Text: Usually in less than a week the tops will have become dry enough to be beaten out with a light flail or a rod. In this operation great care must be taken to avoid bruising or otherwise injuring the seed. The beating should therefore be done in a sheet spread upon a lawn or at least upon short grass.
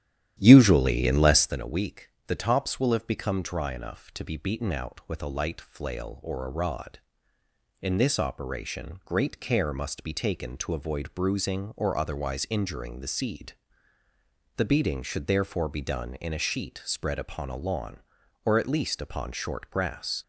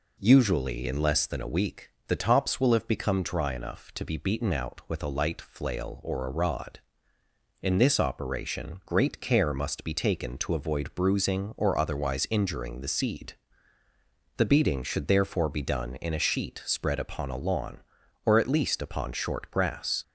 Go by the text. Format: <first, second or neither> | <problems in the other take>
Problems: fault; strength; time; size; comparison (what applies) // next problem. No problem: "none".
second | starts louder than the rest; strong; until 1.6 s; 11.5 dB // pauses between "week" and "the"; slight; at 2.0 s; 0.18 s long; slight in the second